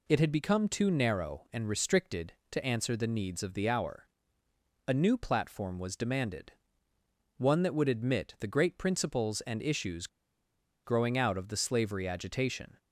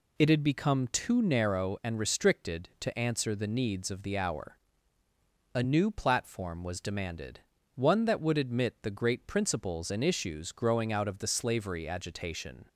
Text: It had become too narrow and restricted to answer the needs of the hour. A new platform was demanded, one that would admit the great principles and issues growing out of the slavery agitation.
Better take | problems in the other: second | pauses between "issues" and "growing"; noticeable; at 10.0 s; 0.78 s long

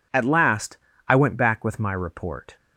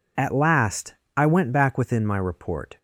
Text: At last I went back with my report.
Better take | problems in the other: first | pauses between "last" and "I"; slight; at 0.9 s; 0.22 s long; slight in the first // says "within" for "with"; at 1.7 s

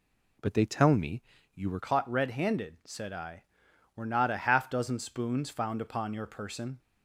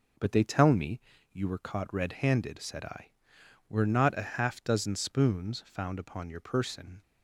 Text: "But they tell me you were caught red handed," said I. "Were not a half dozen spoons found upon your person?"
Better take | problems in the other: second | pauses between "me" and "you"; slight; at 1.2 s; 0.36 s long; slight in the second // changes voice at "caught"; from 1.8 s on; 4.9 s long

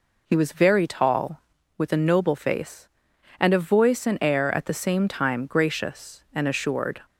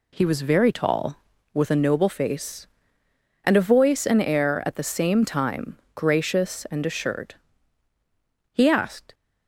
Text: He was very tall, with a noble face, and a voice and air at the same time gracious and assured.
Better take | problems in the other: first | pauses between "time" and "gracious"; slight; at 5.7 s; 0.20 s long // goes on to say "He asked"; noticeable; from 8.5 s on; 0.62 s long

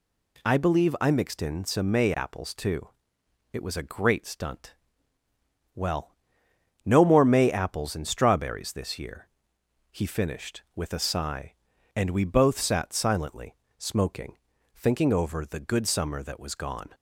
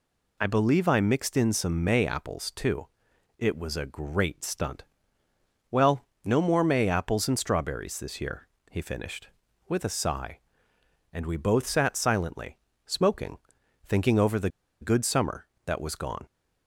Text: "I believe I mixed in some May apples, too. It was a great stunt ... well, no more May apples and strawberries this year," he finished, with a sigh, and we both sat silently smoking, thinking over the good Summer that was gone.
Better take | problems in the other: first | pauses between "silently" and "smoking"; slight; at 12.5 s; 0.28 s long; slight in the first // pauses between "the" and "good"; slight; at 14.4 s; 0.32 s long

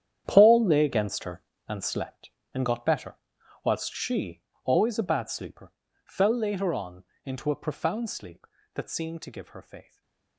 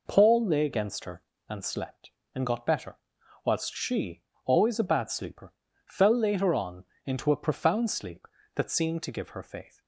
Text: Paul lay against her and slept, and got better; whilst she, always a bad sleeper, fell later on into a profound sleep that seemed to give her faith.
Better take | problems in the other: second | gets quieter; strong; throughout; 15 dB // pauses between "on" and "into"; slight; at 7.0 s; 0.22 s long; slight in the second // stays silent after the last word; slight; from 9.8 s on; 0.5 s long

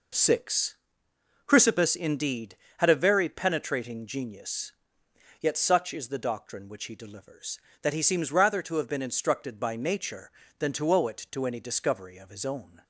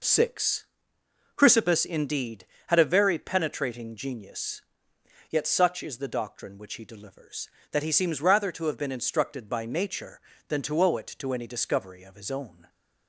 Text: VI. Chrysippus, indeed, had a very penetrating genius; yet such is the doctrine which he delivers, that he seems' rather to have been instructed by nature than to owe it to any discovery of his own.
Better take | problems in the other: neither | none

